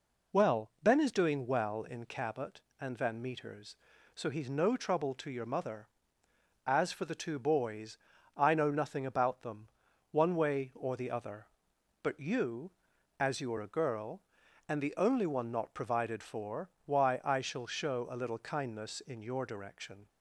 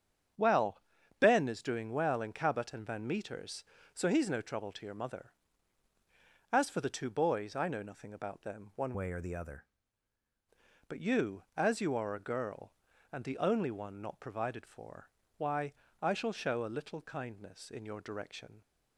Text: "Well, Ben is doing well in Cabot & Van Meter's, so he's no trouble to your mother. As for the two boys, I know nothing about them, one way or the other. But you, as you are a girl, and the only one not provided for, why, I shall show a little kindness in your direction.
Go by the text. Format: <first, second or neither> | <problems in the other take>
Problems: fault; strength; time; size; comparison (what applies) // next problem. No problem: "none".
first | starts louder than the rest; strong; until 1.7 s; 8 dB // changes voice from "way" to "other"; from 8.9 to 9.6 s; 0.7 s long